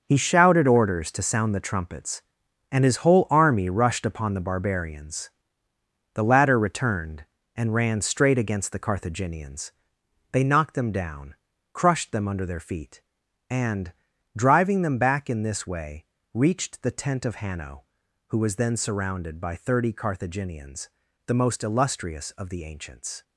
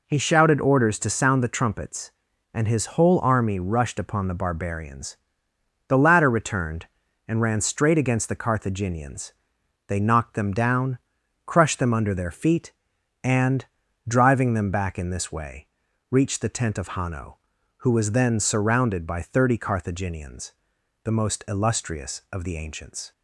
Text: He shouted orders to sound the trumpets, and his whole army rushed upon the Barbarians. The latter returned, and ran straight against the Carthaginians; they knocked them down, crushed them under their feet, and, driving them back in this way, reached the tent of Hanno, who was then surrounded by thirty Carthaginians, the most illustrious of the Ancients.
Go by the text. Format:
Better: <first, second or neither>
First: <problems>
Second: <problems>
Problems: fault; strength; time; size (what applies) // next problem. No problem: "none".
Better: second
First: gets quieter; strong; throughout; 10.5 dB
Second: none